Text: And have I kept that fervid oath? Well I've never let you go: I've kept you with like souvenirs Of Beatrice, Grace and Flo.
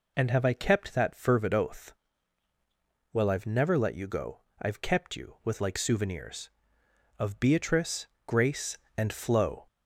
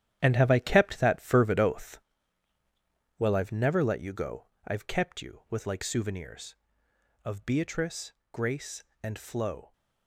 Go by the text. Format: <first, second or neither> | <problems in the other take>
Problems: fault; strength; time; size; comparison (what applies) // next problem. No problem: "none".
first | gets quieter; strong; throughout; 10.5 dB